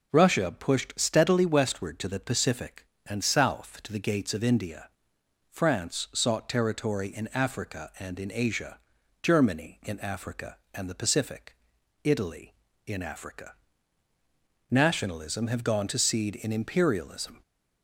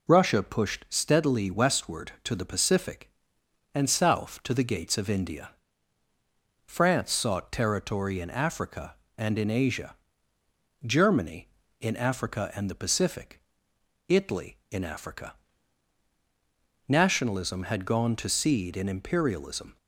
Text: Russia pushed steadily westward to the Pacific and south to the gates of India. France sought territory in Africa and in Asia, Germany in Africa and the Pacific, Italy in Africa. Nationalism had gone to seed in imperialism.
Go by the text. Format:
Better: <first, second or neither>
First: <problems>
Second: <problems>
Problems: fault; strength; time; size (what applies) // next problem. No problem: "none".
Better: second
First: says "have" for "had"; at 15.4 s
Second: none